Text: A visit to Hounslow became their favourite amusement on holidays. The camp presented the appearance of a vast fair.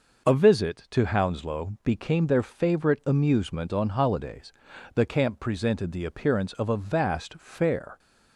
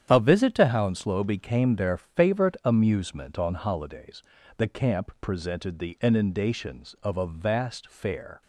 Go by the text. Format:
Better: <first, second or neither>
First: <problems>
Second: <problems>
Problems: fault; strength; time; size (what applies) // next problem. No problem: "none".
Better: first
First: none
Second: starts louder than the rest; strong; until 1.1 s; 9.5 dB // says "inundations" for "appearance"; at 6.0 s